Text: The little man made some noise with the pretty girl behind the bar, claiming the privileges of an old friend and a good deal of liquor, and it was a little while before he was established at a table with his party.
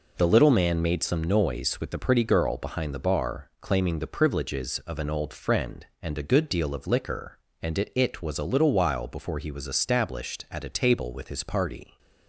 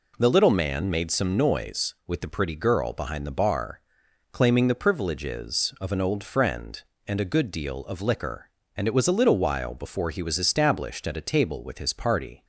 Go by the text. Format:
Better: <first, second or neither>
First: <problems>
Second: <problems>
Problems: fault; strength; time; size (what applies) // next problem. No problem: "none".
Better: second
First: says "it" twice; at 7.9 s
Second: none